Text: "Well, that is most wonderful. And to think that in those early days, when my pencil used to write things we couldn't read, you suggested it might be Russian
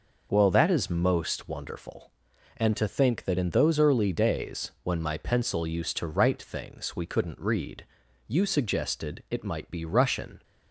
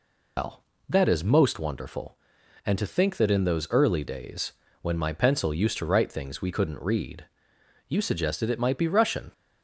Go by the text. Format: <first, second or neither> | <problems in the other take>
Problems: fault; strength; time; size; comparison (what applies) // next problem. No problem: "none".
first | loses the start of "Well"; at 0.3 s; 150 ms